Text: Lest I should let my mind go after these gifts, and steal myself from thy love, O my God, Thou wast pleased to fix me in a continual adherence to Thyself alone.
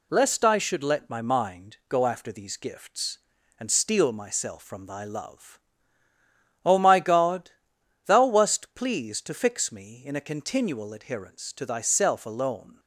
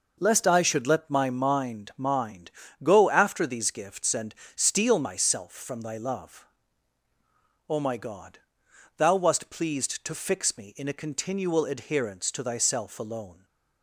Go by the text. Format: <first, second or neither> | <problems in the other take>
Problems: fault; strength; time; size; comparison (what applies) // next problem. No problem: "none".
first | says "mind" twice; at 1.9 s // pauses between "and" and "steal"; slight; at 4.3 s; 0.22 s long